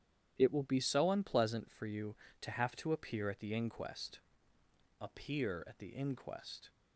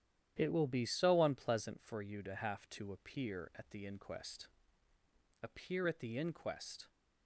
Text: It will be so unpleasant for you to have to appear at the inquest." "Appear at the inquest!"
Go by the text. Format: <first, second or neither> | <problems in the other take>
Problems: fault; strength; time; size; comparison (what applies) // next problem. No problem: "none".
neither | starts louder than the rest; strong; the same in both